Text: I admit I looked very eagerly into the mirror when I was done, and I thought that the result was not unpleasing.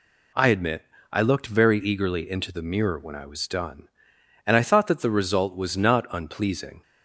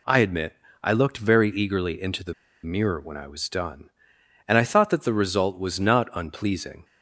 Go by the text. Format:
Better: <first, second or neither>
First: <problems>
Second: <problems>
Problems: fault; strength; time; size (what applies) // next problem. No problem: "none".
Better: first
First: pauses between "admit" and "I"; slight; at 0.8 s; 0.26 s long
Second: pauses between "admit" and "I"; slight; at 0.5 s; 0.26 s long // pauses between "the" and "mirror"; slight; at 2.3 s; 0.30 s long